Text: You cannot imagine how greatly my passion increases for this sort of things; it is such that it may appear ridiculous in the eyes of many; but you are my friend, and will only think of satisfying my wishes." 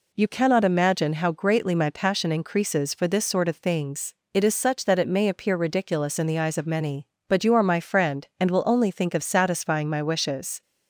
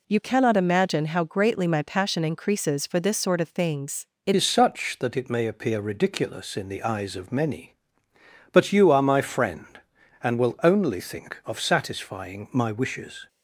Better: first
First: none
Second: changes voice at "is"; from 4.3 s on; 8.9 s long

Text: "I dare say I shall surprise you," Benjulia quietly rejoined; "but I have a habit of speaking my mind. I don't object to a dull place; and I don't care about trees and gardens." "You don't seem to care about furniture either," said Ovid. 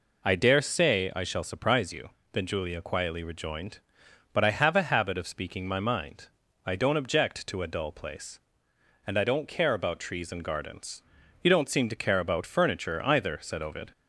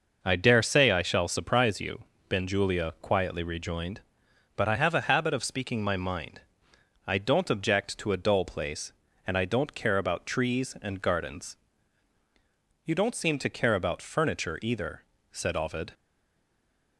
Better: first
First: none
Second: stays silent after the last word; from 15.9 s on; 1.0 s long

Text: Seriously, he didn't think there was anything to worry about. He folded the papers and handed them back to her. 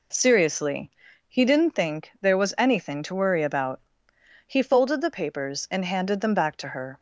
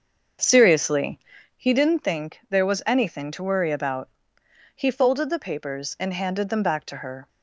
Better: first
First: none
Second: starts louder than the rest; until 1.7 s; 6.5 dB

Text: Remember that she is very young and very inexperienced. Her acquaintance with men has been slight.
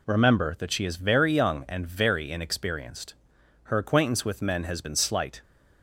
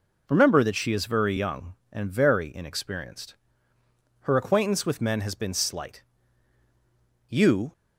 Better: first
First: none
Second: goes on to say "You"; slight; from 7.2 s on; 0.44 s long

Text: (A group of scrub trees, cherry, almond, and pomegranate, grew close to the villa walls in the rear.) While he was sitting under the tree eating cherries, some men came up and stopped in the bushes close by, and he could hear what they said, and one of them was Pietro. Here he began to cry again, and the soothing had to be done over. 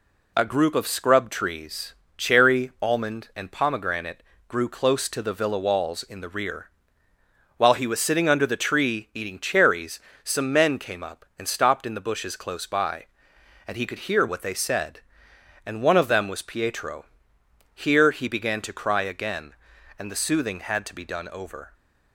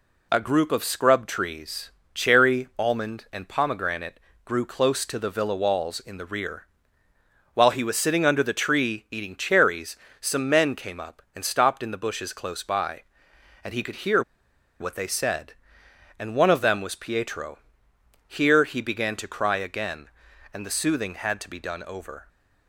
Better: first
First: none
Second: pauses between "hear" and "what"; noticeable; at 14.2 s; 0.59 s long

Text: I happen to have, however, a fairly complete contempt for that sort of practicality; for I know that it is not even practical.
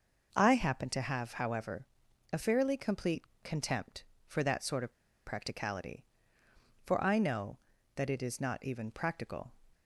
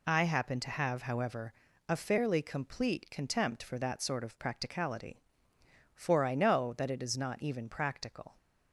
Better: second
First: pauses between "complete" and "contempt"; slight; at 3.2 s; 0.20 s long // pauses between "of" and "practicality"; slight; at 4.9 s; 0.34 s long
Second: none

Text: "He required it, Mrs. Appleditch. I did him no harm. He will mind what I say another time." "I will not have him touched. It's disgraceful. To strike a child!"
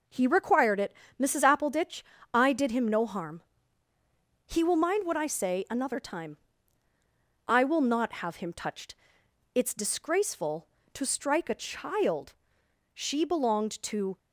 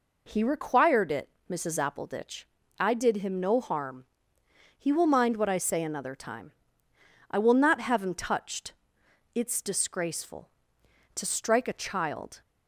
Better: second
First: goes on to say "She belonged to"; noticeable; from 12.9 s on; 1.2 s long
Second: none

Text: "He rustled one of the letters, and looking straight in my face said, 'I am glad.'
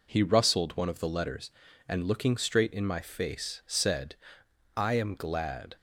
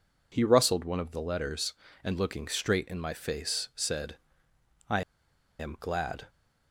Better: first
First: none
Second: pauses between "I" and "am"; noticeable; at 5.0 s; 0.58 s long

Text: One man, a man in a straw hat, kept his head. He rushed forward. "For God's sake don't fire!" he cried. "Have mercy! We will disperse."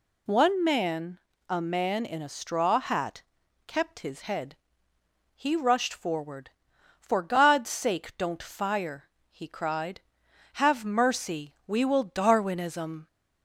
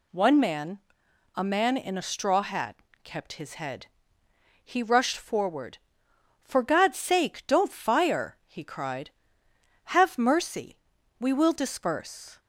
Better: second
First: says "darwinism" for "disperse"; at 12.0 s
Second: none

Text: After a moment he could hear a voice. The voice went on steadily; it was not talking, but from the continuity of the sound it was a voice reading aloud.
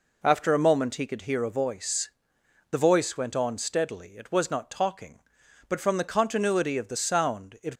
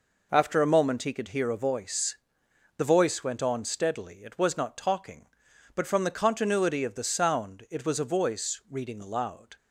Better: second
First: stops before "was a voice reading aloud"; at 7.7 s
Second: none

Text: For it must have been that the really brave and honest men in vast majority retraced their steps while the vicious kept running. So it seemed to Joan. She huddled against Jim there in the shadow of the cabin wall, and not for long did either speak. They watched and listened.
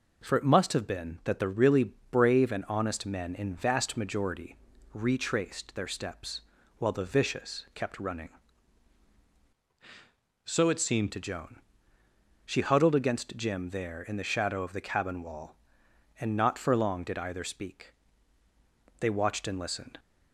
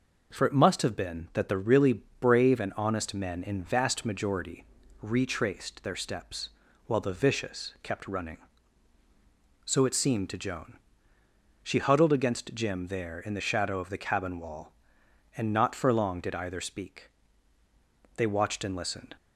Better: second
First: pauses between "really" and "brave"; slight; at 1.9 s; 0.20 s long // pauses between "majority" and "retraced"; at 4.5 s; 0.38 s long // pauses between "steps" and "while"; at 6.4 s; 0.38 s long // changes voice from "So" to "seemed"; from 10.4 to 11.1 s; 0.7 s long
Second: pauses between "really" and "brave"; slight; at 2.0 s; 0.20 s long // pauses between "majority" and "retraced"; at 4.6 s; 0.38 s long // pauses between "steps" and "while"; at 6.4 s; 0.38 s long

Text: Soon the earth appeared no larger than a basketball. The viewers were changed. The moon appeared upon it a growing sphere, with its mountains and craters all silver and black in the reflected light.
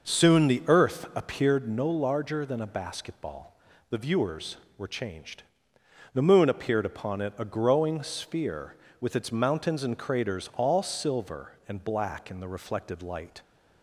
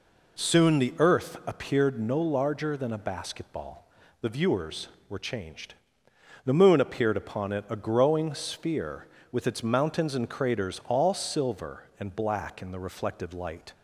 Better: second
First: starts louder than the rest; noticeable; until 1.5 s; 6 dB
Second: none

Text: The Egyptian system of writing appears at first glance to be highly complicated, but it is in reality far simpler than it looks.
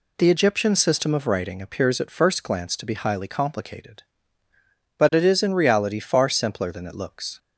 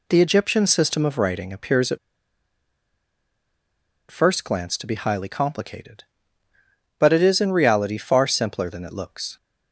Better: first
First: none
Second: pauses between "at" and "first"; strong; at 1.9 s; 2.1 s long

